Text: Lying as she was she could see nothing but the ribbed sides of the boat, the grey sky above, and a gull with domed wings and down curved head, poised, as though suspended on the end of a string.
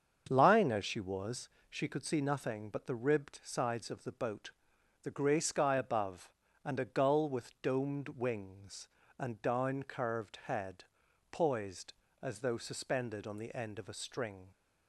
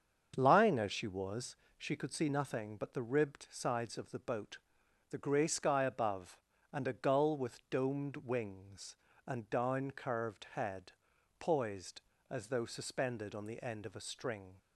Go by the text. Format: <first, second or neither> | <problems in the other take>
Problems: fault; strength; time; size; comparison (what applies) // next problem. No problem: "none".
neither | starts louder than the rest; the same in both // pauses between "was" and "she"; slight; the same in both